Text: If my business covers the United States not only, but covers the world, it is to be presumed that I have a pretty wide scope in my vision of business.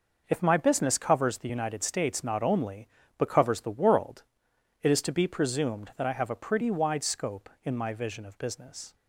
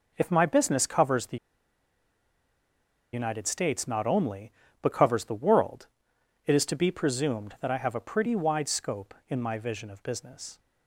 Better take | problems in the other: first | pauses between "the" and "United"; strong; at 1.3 s; 1.7 s long

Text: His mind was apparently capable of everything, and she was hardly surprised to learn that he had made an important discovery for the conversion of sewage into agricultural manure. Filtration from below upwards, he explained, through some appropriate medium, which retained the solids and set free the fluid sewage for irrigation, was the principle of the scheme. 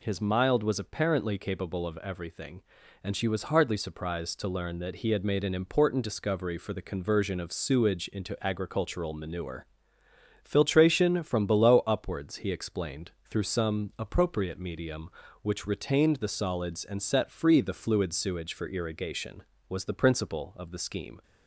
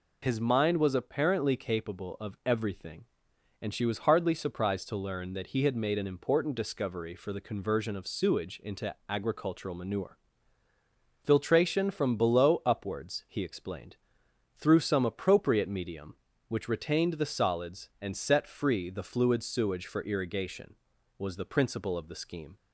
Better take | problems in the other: second | says "mild" for "mind"; at 0.2 s

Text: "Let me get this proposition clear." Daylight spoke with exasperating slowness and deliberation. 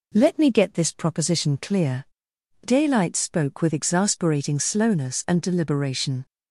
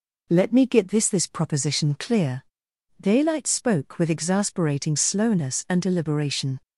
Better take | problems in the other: first | says "this" twice; at 1.0 s

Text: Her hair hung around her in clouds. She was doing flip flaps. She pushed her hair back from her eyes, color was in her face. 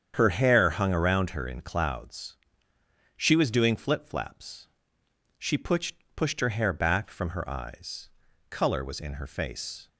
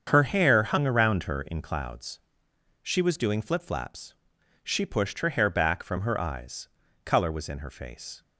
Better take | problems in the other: second | starts louder than the rest; strong; until 1.1 s; 8 dB; strong in the second // says "pushed" twice; at 6.1 s

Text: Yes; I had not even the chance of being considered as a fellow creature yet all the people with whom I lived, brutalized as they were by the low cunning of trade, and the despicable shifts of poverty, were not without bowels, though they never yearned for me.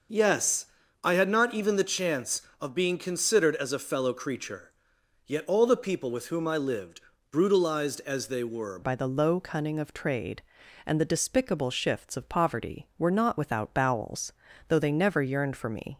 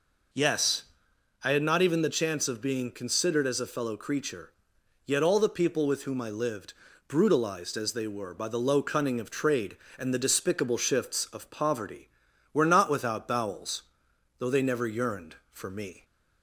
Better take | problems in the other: second | starts louder than the rest; noticeable; until 1.5 s; 6 dB // pauses between "creature" and "yet"; noticeable; at 4.7 s; 0.56 s long; noticeable in the second // changes voice at "by"; from 8.8 s on; 7.1 s long

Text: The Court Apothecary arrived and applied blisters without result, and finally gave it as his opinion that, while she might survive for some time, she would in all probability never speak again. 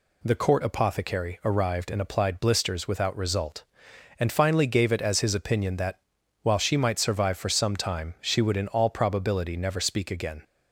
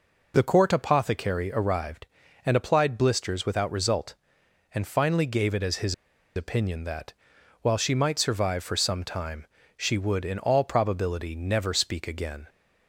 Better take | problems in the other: first | pauses between "his" and "opinion"; at 5.9 s; 0.42 s long

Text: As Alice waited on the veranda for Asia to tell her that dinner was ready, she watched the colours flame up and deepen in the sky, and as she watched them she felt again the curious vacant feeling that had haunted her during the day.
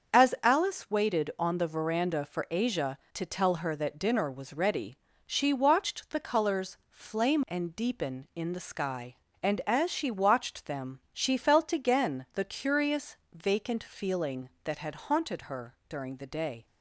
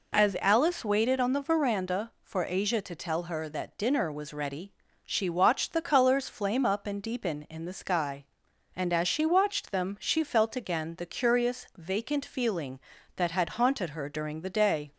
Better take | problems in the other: second | starts louder than the rest; until 1.2 s; 7 dB // skips "up"; at 7.4 s // pauses between "curious" and "vacant"; slight; at 13.1 s; 0.16 s long

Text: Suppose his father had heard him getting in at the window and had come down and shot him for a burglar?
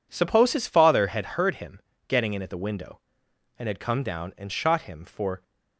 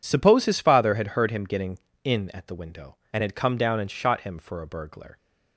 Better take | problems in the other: second | pauses between "him" and "getting"; slight; at 1.7 s; 0.28 s long // stops before "a burglar"; at 5.4 s

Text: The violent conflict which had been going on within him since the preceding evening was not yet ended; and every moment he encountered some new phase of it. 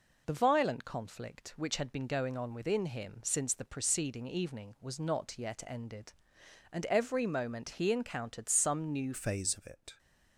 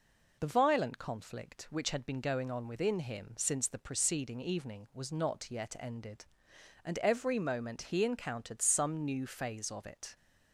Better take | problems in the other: second | changes voice at "phase"; from 9.1 s on; 0.8 s long

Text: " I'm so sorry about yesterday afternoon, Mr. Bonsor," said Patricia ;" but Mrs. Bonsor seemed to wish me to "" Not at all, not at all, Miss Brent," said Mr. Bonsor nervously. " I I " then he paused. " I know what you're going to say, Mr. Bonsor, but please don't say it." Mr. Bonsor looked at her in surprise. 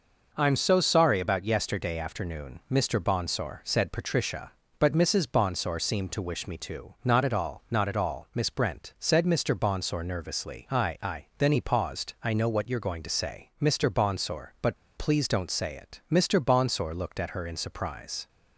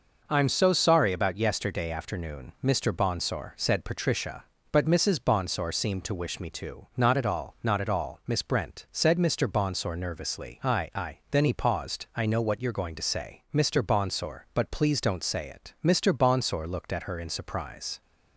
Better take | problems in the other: second | pauses between "but" and "please"; slight; at 14.7 s; 0.20 s long

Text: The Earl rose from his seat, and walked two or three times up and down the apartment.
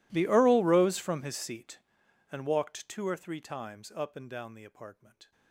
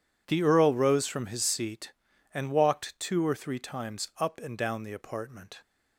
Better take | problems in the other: second | gets quieter; strong; throughout; 29.5 dB

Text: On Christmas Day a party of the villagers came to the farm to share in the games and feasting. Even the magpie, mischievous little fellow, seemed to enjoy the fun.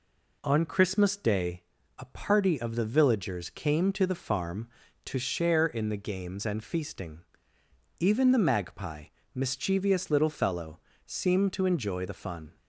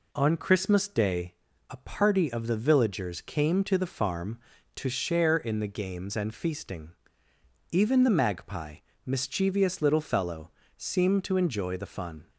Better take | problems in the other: neither | pauses between "Day" and "a"; slight; the same in both

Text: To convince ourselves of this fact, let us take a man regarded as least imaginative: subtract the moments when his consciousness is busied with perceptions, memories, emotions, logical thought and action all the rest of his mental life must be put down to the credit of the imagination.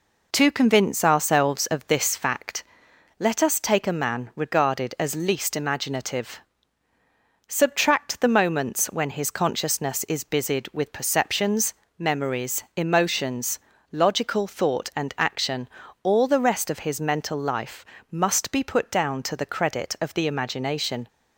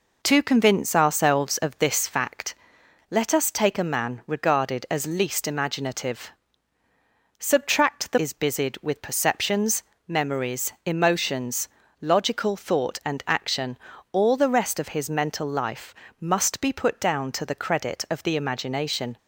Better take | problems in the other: first | skips "moments when his consciousness"; at 8.1 s // pauses between "action" and "all"; slight; at 13.7 s; 0.36 s long; slight in the first // pauses between "life" and "must"; slight; at 15.9 s; 0.28 s long; slight in the first

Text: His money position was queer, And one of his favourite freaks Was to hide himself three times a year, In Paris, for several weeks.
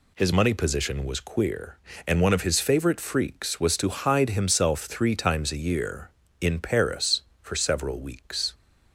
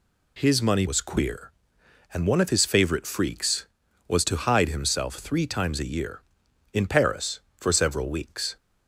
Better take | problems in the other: first | skips "position"; at 0.8 s

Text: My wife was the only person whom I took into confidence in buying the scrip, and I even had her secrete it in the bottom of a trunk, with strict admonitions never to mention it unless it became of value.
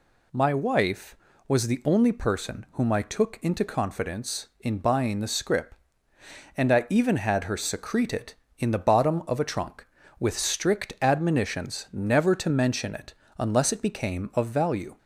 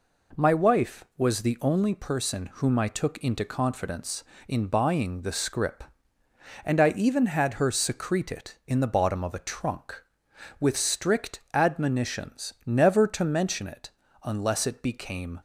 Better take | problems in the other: first | pauses between "it" and "unless"; slight; at 13.9 s; 0.32 s long; slight in the first // stops before "of value"; at 15.3 s

